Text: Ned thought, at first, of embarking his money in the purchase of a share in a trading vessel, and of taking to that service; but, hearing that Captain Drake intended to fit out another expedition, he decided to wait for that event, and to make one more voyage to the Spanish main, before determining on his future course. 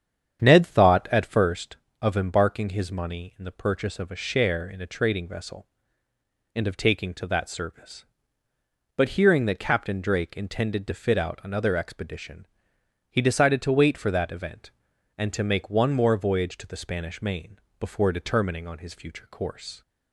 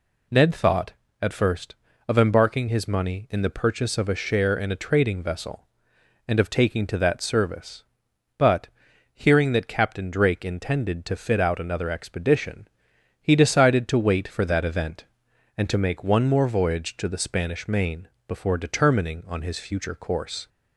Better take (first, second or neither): second